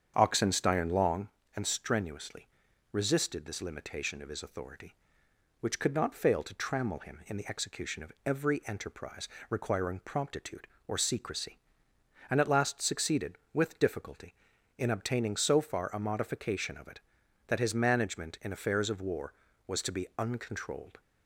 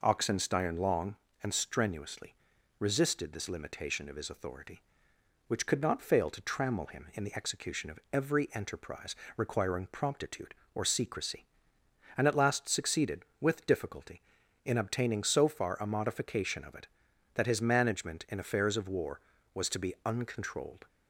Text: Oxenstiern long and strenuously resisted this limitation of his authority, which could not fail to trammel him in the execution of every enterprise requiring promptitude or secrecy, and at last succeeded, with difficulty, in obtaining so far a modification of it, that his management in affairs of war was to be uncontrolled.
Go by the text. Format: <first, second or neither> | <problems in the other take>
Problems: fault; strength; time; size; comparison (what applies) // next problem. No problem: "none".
second | starts louder than the rest; strong; until 1.2 s; 8 dB // pauses between "strenuously" and "resisted"; at 2.4 s; 0.44 s long; also in the second // pauses between "enterprise" and "requiring"; slight; at 9.2 s; 0.22 s long; slight in the second